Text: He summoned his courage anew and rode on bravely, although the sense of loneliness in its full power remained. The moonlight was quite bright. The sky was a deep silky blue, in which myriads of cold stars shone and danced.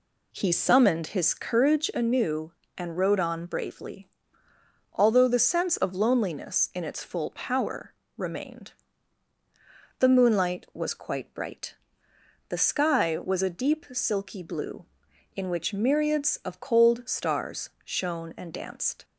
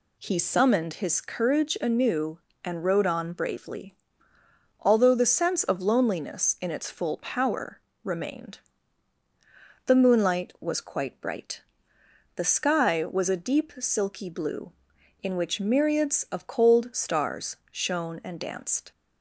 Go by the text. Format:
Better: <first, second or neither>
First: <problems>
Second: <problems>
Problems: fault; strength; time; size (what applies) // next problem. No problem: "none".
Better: second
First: starts louder than the rest; slight; until 2.0 s; 2.5 dB // pauses between "power" and "remained"; slight; at 7.9 s; 0.24 s long // pauses between "stars" and "shone"; slight; at 17.6 s; 0.16 s long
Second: pauses between "power" and "remained"; slight; at 7.7 s; 0.24 s long // pauses between "stars" and "shone"; slight; at 17.5 s; 0.16 s long